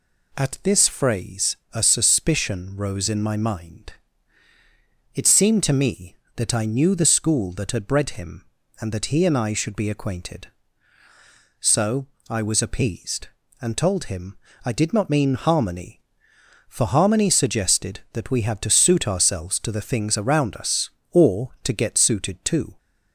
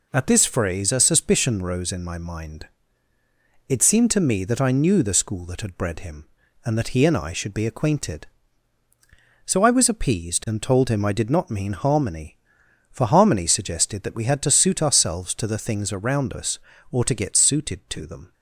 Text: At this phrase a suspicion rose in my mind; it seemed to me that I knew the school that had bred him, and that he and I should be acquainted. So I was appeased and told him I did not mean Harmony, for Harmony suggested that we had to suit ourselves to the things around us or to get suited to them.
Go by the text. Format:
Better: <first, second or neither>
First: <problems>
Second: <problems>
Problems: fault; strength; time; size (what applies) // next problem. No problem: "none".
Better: second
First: pauses between "phrase" and "a"; slight; at 1.5 s; 0.16 s long // pauses between "So" and "I"; slight; at 12.0 s; 0.24 s long // pauses between "him" and "I"; slight; at 14.3 s; 0.26 s long // stops before "them"; at 22.7 s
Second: none